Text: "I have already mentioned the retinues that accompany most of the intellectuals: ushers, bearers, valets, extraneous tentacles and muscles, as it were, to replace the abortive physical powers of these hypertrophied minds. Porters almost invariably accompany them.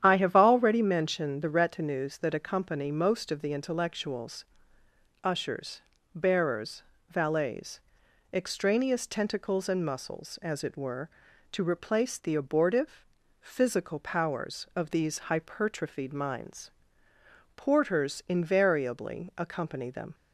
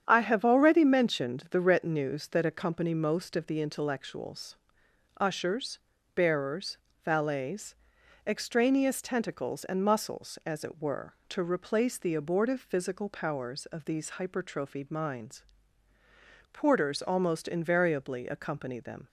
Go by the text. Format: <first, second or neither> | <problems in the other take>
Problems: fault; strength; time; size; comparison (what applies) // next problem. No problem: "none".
second | starts louder than the rest; strong; until 1.0 s; 9.5 dB; strong in the second // pauses between "abortive" and "physical"; at 13.0 s; 0.38 s long // skips "almost"; at 18.2 s